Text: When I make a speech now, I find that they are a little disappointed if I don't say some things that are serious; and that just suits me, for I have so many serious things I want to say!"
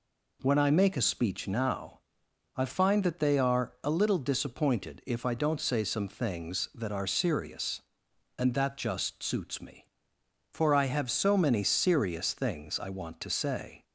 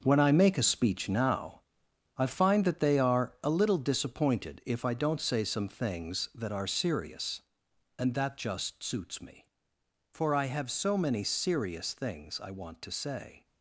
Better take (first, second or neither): first